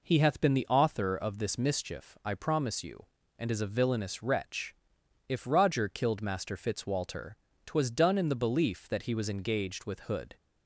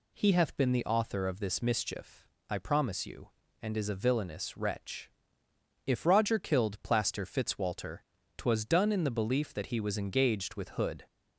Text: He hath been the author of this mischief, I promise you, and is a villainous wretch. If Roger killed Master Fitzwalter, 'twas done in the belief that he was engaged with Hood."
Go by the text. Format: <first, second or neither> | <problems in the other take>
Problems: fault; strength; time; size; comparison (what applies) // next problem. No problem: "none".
first | says "Plaster" for "Master"; at 6.8 s